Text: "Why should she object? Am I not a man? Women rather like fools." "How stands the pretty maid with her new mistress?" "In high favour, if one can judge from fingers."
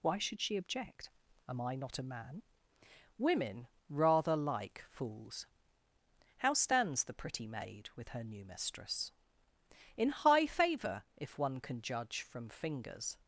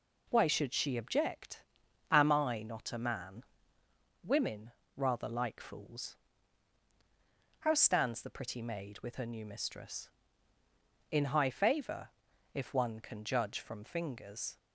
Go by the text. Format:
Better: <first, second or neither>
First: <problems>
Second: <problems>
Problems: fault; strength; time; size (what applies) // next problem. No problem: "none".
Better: neither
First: pauses between "Women" and "rather"; slight; at 3.6 s; 0.20 s long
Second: pauses between "Women" and "rather"; slight; at 4.7 s; 0.26 s long